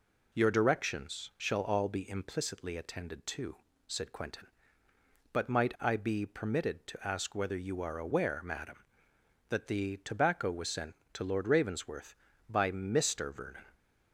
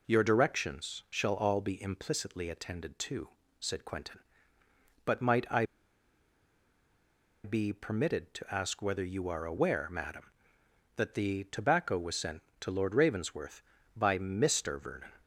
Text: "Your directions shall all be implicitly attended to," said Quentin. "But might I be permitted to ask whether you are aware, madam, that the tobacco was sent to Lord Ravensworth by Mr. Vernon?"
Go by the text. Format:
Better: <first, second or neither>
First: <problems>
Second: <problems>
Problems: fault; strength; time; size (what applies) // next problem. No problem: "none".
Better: first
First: none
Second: pauses between "I" and "be"; strong; at 5.6 s; 1.7 s long